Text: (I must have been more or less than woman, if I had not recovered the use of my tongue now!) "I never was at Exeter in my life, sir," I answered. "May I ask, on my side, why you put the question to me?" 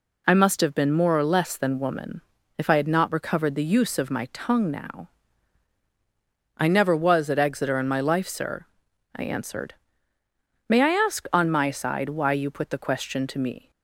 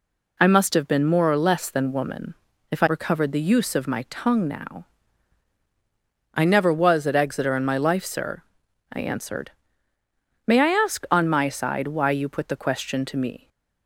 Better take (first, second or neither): first